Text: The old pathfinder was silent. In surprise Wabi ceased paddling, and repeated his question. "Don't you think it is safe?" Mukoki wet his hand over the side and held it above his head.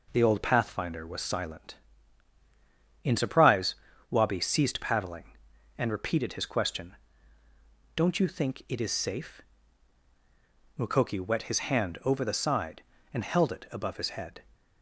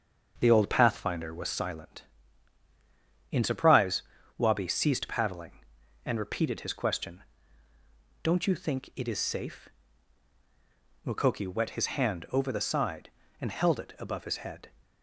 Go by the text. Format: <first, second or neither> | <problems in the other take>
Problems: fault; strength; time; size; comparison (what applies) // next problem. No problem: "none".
first | starts louder than the rest; until 1.6 s; 6.5 dB // pauses between "surprise" and "Wabi"; slight; at 4.0 s; 0.34 s long; slight in the first